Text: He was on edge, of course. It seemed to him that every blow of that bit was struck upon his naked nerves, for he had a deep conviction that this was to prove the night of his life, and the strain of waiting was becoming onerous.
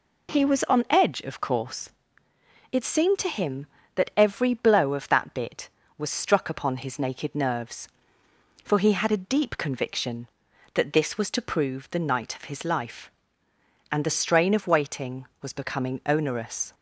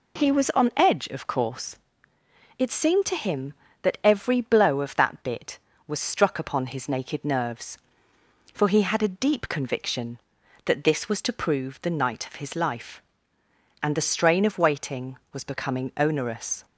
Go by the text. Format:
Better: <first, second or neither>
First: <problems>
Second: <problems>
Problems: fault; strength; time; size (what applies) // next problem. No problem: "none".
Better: neither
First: none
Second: none